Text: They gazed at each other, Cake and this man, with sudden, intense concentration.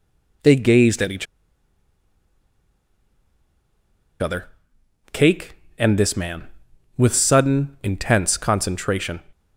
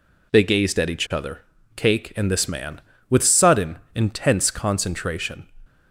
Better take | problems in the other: second | pauses between "each" and "other"; strong; at 1.2 s; 2.9 s long

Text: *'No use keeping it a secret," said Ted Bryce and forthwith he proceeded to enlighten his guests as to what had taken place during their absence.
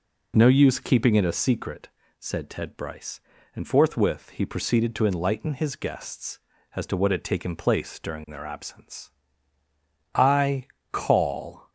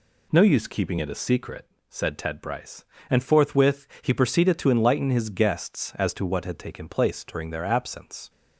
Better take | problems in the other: second | goes on to say "I call"; from 10.1 s on; 1.5 s long

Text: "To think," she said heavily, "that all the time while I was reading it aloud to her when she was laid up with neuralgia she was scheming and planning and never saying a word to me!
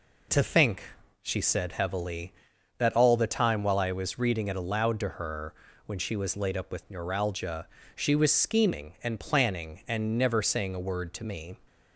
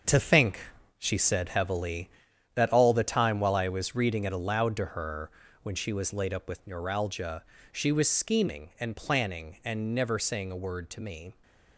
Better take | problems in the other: first | gets quieter; strong; throughout; 9 dB // pauses between "her" and "when"; slight; at 5.3 s; 0.32 s long; slight in the first // pauses between "neuralgia" and "she"; slight; at 7.4 s; 0.30 s long; slight in the first

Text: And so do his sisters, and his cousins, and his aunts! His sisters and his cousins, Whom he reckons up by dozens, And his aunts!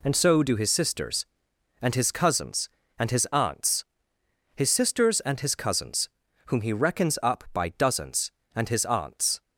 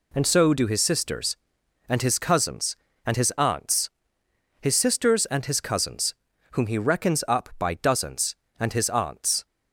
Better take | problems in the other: neither | none

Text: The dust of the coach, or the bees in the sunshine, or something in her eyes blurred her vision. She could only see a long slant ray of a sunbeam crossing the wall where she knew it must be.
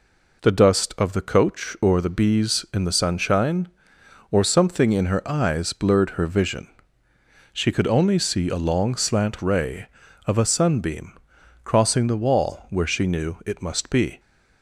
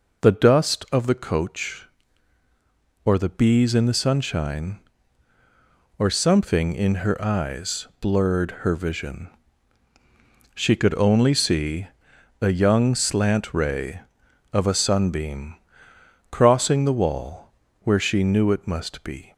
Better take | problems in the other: first | pauses between "see" and "a"; noticeable; at 11.8 s; 0.52 s long // says "young" for "long"; at 12.5 s // pauses between "sunbeam" and "crossing"; noticeable; at 15.5 s; 0.76 s long; noticeable in the first // pauses between "wall" and "where"; slight; at 17.5 s; 0.34 s long

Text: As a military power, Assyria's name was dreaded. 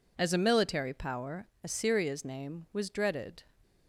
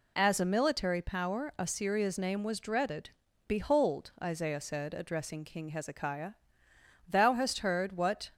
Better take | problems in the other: first | goes on to say "Behold Isaiah said addressing King Hezekiah thou hast heard what"; strong; from 3.4 s on; 4.8 s long

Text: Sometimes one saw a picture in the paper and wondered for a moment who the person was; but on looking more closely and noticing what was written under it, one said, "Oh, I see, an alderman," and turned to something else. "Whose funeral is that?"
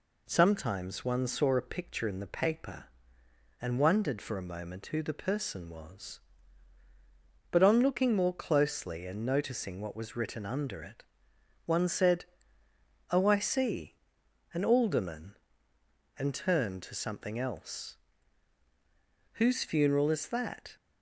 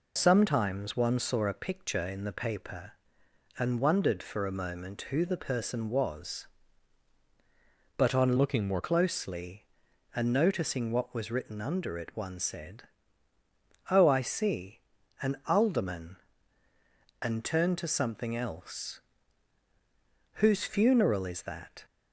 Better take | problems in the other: first | changes voice from "looking" to "more"; from 8.3 to 8.8 s; 0.5 s long

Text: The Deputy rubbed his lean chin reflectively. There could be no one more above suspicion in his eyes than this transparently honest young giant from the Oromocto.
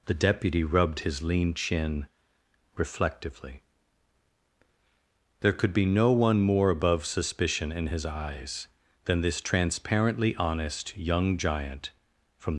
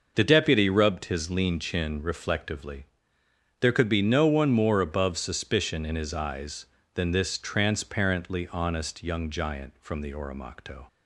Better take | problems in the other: second | pauses between "chin" and "reflectively"; noticeable; at 2.0 s; 0.68 s long // stops before "the Oromocto"; at 12.5 s

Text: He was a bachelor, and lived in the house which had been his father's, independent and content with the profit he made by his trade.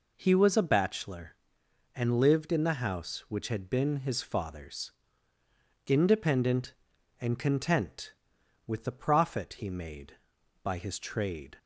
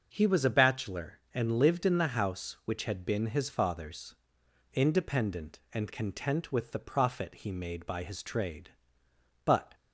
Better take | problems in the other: first | starts louder than the rest; until 1.1 s; 6.5 dB // goes on to say "But"; slight; from 9.4 s on; 0.30 s long

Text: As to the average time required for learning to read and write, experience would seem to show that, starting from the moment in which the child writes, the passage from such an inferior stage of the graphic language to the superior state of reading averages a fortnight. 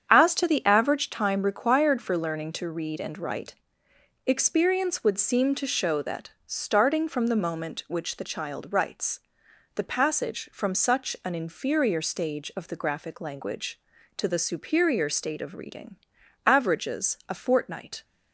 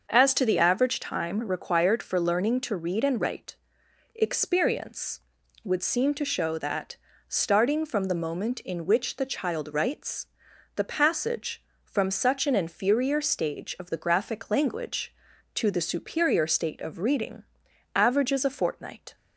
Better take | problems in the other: second | starts louder than the rest; strong; until 1.1 s; 8 dB; also in the second // skips "in"; at 7.8 s // pauses between "reading" and "averages"; noticeable; at 15.9 s; 0.50 s long; noticeable in the second

